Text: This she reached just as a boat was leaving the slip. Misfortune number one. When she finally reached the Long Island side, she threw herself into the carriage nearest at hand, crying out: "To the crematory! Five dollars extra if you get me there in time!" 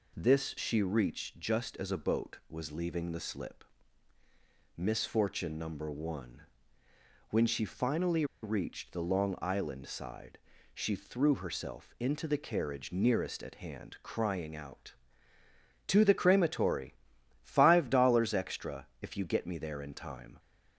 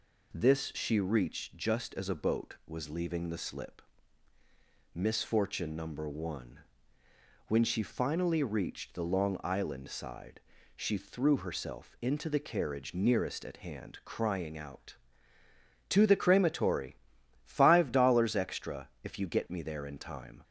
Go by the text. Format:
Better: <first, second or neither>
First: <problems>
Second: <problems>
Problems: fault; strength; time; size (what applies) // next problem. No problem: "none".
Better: second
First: pauses between "finally" and "reached"; slight; at 8.2 s; 0.18 s long // pauses between "extra" and "if"; slight; at 18.8 s; 0.16 s long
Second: pauses between "extra" and "if"; slight; at 18.8 s; 0.16 s long